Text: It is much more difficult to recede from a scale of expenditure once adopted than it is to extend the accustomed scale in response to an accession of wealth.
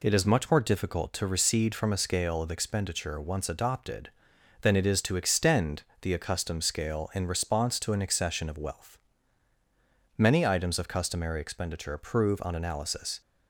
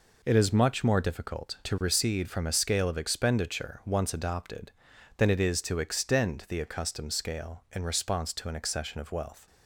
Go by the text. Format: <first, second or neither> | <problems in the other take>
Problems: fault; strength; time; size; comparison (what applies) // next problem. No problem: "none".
second | pauses between "extend" and "the"; slight; at 5.8 s; 0.18 s long // goes on to say "Many items of customary expenditure prove on analysis"; strong; from 10.1 s on; 3.0 s long